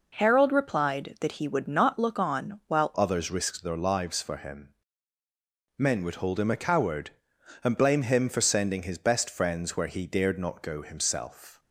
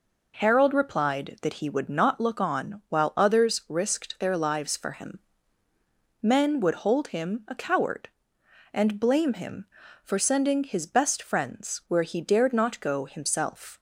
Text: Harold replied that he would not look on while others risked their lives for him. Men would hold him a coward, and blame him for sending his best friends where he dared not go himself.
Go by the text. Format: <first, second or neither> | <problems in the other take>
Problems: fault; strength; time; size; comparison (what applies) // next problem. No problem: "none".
second | changes voice at "others"; from 2.9 s on; 8.6 s long